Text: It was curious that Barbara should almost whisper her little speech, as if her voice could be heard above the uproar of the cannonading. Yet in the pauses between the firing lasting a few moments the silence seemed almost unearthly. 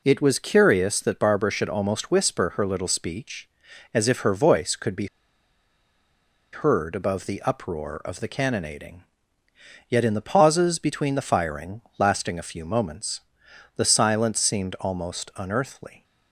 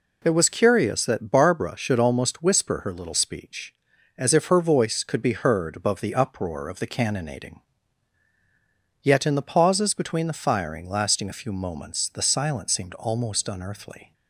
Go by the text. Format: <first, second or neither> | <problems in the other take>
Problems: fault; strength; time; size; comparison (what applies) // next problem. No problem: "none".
second | pauses between "be" and "heard"; strong; at 5.0 s; 1.4 s long // pauses between "firing" and "lasting"; slight; at 11.8 s; 0.18 s long // pauses between "moments" and "the"; noticeable; at 13.2 s; 0.56 s long